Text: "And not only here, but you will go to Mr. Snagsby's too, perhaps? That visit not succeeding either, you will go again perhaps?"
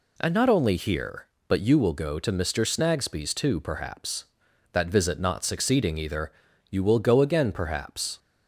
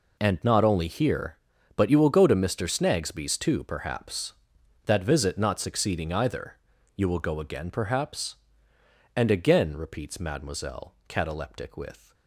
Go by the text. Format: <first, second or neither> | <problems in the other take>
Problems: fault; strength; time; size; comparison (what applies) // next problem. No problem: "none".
first | goes on to say "And again repeats mademoiselle cataleptic with"; strong; from 9.1 s on; 3.0 s long